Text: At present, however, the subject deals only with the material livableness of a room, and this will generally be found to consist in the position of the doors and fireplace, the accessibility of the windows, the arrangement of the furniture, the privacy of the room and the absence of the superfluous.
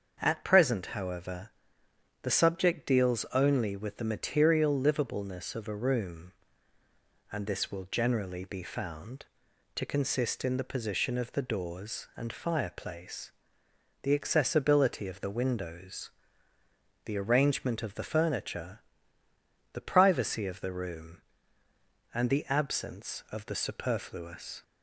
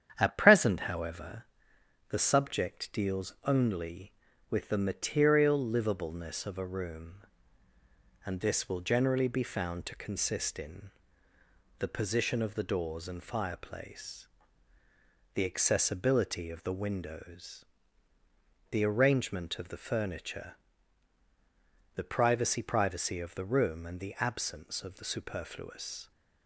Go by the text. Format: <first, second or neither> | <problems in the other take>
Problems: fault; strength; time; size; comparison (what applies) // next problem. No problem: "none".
first | starts louder than the rest; strong; until 1.1 s; 9 dB; also in the first // pauses between "in" and "the"; noticeable; at 10.9 s; 0.88 s long // says "privacy" twice; at 22.6 s